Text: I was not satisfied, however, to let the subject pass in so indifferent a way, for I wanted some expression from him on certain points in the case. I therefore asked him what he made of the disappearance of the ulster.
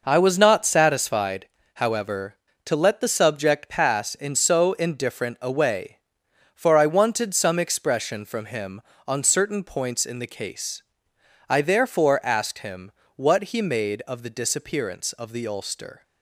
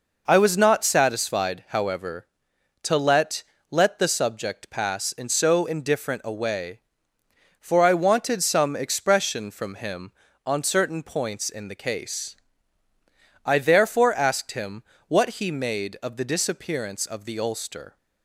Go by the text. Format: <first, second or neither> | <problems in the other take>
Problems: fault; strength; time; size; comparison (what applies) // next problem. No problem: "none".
first | says "let" twice; at 3.6 s // pauses between "him" and "what"; slight; at 14.8 s; 0.26 s long; slight in the first